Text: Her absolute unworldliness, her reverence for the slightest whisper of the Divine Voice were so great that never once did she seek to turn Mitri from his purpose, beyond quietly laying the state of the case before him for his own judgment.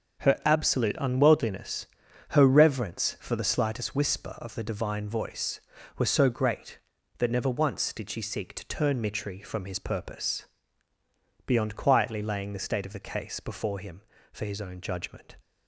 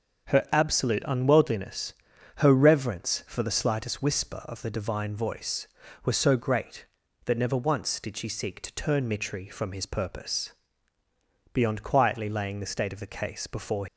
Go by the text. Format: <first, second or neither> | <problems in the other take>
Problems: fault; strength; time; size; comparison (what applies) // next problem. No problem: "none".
first | starts louder than the rest; until 1.3 s; 6.5 dB; also in the first // stops before "him for his own judgment"; at 13.8 s